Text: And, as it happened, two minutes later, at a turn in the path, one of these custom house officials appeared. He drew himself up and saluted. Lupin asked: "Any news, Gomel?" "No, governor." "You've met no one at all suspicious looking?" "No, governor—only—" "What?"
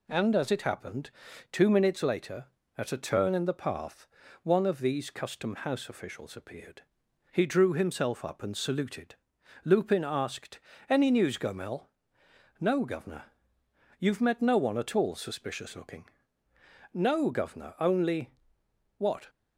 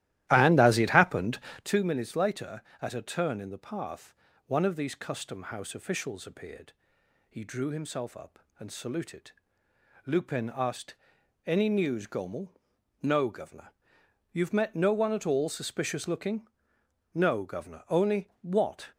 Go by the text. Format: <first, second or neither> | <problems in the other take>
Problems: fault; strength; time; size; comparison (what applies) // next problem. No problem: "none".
first | starts louder than the rest; strong; until 1.7 s; 15 dB